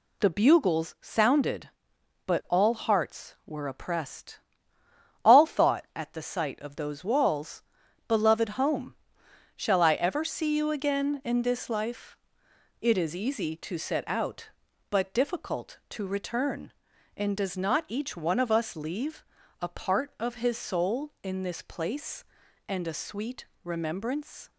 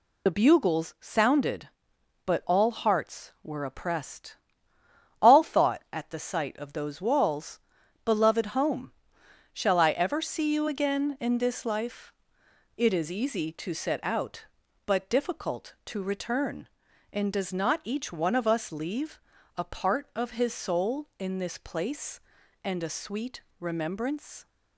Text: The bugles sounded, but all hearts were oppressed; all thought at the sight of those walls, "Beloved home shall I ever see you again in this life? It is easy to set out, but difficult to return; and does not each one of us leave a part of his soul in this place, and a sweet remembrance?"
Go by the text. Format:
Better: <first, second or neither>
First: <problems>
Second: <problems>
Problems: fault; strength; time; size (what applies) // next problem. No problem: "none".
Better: first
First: pauses between "home" and "shall"; noticeable; at 8.9 s; 0.62 s long // pauses between "leave" and "a"; slight; at 19.2 s; 0.34 s long // pauses between "sweet" and "remembrance"; slight; at 23.4 s; 0.18 s long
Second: loses the start of "The"; at 0.2 s; 45 ms // pauses between "home" and "shall"; noticeable; at 8.9 s; 0.62 s long // pauses between "leave" and "a"; slight; at 19.2 s; 0.34 s long // pauses between "sweet" and "remembrance"; slight; at 23.4 s; 0.18 s long